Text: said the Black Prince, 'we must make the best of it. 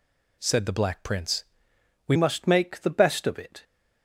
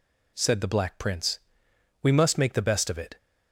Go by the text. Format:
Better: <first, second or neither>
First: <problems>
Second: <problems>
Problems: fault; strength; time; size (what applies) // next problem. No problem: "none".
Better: second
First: changes voice at "must"; from 2.1 s on; 1.5 s long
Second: none